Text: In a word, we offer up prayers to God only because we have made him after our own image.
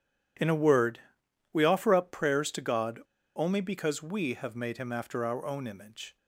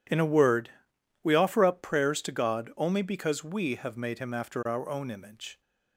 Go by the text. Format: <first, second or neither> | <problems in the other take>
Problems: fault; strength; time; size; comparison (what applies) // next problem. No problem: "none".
second | pauses between "God" and "only"; at 2.9 s; 0.37 s long